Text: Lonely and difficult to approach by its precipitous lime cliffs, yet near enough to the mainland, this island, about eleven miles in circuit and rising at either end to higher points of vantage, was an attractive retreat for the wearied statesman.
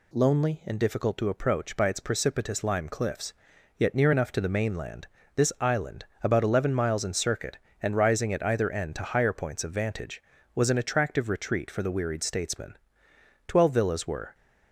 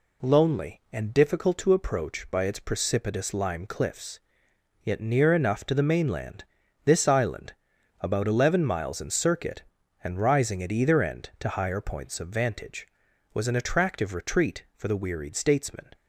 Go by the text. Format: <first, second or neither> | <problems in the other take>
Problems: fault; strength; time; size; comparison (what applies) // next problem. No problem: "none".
second | goes on to say "Twelve villas were"; noticeable; from 13.4 s on; 0.88 s long